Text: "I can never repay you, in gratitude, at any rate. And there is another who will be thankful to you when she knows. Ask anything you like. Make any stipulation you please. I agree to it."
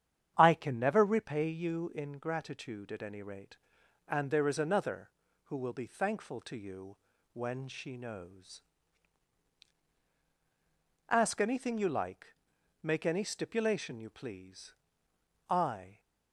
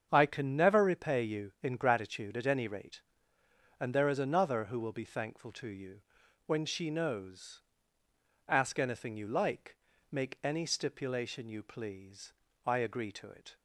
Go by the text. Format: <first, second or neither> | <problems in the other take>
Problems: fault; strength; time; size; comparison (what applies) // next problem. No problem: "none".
second | starts louder than the rest; strong; until 1.3 s; 9 dB; strong in the second // pauses between "you" and "when"; at 6.9 s; 0.38 s long; noticeable in the second // stops before "agree to it"; at 15.9 s